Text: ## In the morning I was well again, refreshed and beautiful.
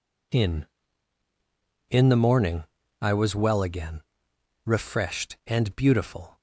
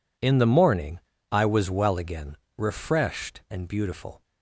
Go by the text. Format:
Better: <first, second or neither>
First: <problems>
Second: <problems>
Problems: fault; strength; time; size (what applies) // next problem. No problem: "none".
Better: second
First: says "In" twice; at 1.8 s // pauses between "morning" and "I"; slight; at 2.6 s; 0.36 s long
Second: pauses between "morning" and "I"; slight; at 0.9 s; 0.32 s long